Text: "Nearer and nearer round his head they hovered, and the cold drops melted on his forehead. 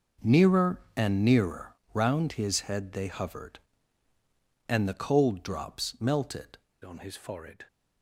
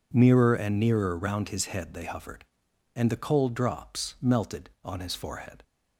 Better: second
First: pauses between "nearer" and "round"; slight; at 1.7 s; 0.16 s long // changes voice at "on"; from 6.8 s on; 0.8 s long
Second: none

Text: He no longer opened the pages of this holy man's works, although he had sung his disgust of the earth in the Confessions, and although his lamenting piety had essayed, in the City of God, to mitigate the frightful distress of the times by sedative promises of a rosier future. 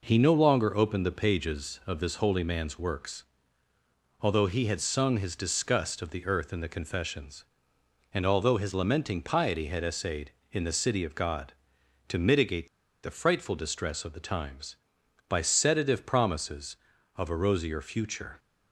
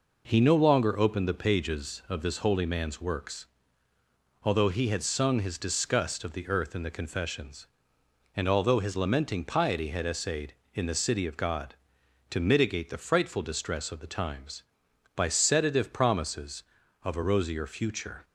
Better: second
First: pauses between "mitigate" and "the"; slight; at 12.6 s; 0.35 s long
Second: none

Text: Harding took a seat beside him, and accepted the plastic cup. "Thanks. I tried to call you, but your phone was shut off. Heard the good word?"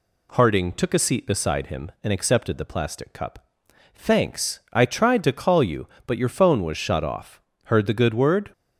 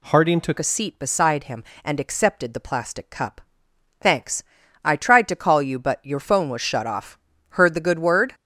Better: first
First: none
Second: changes voice at "a"; from 0.5 s on; 7.8 s long

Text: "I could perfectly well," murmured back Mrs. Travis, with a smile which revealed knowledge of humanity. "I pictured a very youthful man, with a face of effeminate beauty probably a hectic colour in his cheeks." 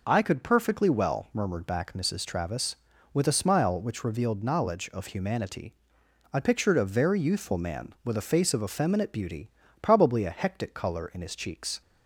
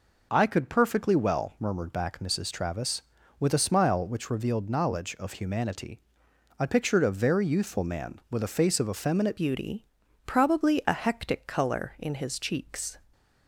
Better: first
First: pauses between "beauty" and "probably"; slight; at 9.4 s; 0.32 s long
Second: changes voice at "beauty"; from 9.3 s on; 3.6 s long // pauses between "beauty" and "probably"; at 9.8 s; 0.42 s long

